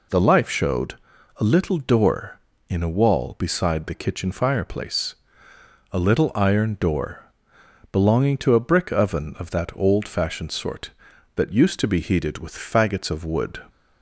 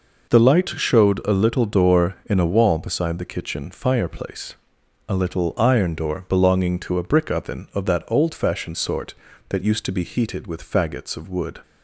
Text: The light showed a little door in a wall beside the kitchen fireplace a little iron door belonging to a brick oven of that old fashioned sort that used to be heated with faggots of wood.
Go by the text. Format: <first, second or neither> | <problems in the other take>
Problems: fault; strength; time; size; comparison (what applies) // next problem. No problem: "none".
second | says "life" for "light"; at 0.2 s // pauses between "showed" and "a"; at 0.9 s; 0.42 s long // pauses between "fireplace" and "a"; noticeable; at 5.1 s; 0.76 s long; noticeable in the second // pauses between "door" and "belonging"; noticeable; at 7.2 s; 0.68 s long